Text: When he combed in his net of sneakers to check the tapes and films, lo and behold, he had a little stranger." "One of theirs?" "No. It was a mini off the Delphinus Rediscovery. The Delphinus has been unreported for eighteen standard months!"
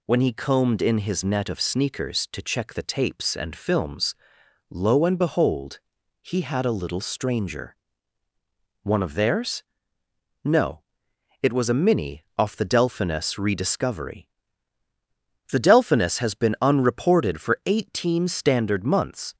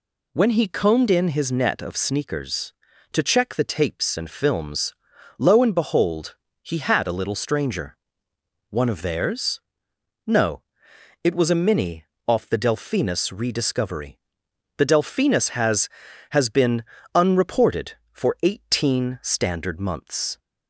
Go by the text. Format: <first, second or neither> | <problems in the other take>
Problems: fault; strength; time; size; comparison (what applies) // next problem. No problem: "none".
first | pauses between "mini" and "off"; slight; at 12.0 s; 0.24 s long // says "has" twice; at 16.2 s // pauses between "been" and "unreported"; slight; at 16.8 s; 0.28 s long